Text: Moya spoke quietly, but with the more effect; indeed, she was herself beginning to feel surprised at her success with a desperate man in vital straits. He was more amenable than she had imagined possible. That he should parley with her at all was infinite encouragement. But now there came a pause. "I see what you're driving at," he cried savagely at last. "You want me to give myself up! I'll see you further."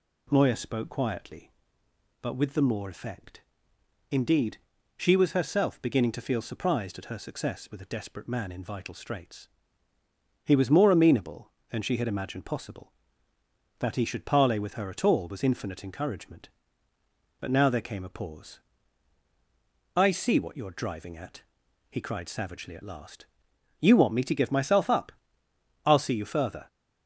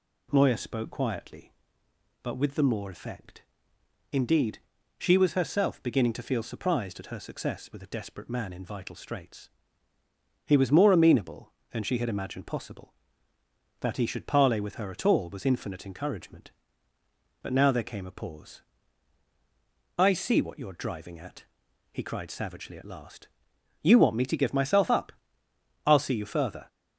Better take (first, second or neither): neither